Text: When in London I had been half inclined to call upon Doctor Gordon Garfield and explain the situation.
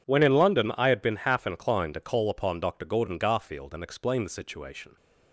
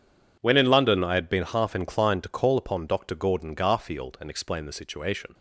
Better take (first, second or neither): neither